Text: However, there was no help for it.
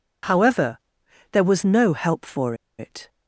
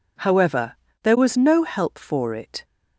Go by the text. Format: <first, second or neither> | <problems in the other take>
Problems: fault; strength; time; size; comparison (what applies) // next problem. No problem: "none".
second | pauses between "for" and "it"; slight; at 2.5 s; 0.24 s long